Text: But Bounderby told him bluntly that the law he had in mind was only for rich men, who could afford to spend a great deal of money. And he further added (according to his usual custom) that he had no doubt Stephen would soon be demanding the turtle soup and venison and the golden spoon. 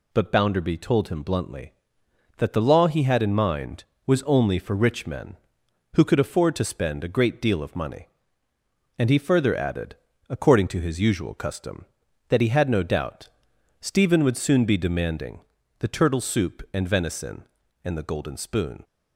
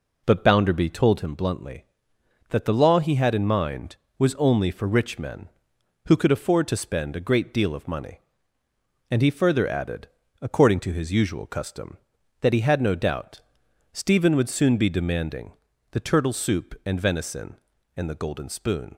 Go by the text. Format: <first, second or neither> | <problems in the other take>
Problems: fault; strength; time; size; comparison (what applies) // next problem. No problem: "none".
first | starts louder than the rest; noticeable; until 1.3 s; 4 dB // pauses between "doubt" and "Stephen"; noticeable; at 13.4 s; 0.50 s long; noticeable in the first // pauses between "demanding" and "the"; at 15.5 s; 0.40 s long; also in the first